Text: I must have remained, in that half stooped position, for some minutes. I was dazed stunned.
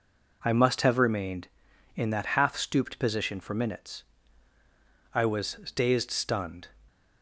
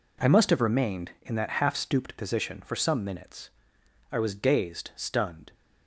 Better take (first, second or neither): second